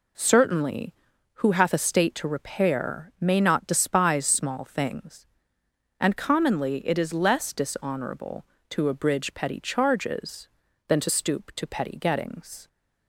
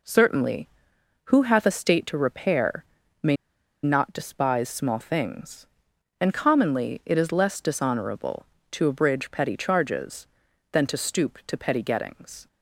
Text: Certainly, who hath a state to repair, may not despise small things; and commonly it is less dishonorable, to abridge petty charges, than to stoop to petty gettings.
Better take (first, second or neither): first